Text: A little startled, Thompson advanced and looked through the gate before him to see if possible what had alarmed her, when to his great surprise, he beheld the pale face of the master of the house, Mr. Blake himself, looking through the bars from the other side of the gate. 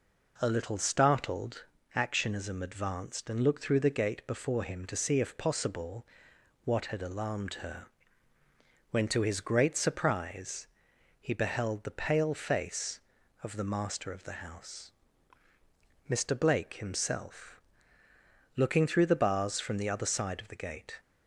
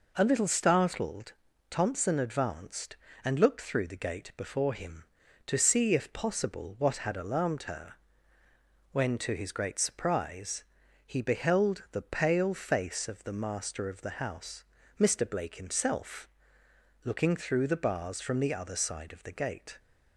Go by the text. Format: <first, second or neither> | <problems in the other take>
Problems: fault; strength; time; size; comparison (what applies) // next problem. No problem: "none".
second | says "Actionism" for "Thompson"; at 1.9 s // pauses between "possible" and "what"; noticeable; at 6.0 s; 0.60 s long